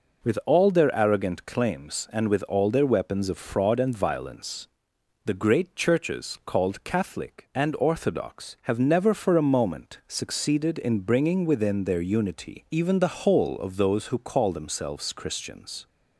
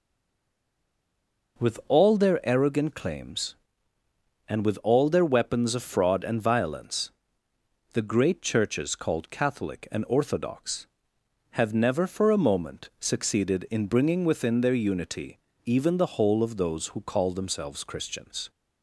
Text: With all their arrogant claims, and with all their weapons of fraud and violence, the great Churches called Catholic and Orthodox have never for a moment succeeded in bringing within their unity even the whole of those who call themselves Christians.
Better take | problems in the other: first | stays silent before the first word; noticeable; until 1.5 s; 1.5 s long // pauses between "unity" and "even"; slight; at 15.3 s; 0.26 s long

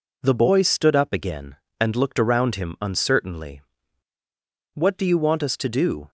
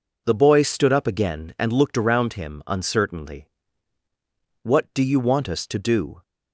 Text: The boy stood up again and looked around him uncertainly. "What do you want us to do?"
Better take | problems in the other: neither | none

